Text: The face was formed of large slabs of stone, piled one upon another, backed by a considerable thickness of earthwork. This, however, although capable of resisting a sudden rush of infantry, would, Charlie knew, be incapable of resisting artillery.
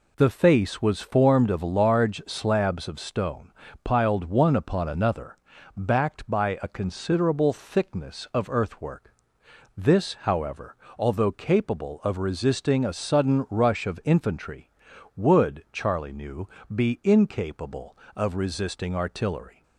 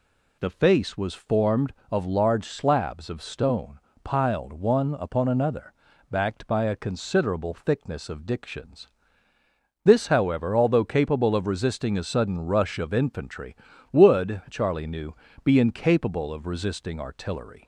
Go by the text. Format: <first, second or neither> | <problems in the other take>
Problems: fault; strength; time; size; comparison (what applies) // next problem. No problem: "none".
first | says "dictions" for "earthwork"; at 8.2 s